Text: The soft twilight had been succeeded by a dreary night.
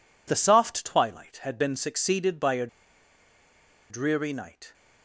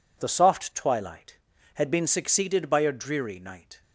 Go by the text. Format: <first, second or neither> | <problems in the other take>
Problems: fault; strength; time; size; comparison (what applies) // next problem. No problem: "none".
second | pauses between "a" and "dreary"; at 2.6 s; 1.2 s long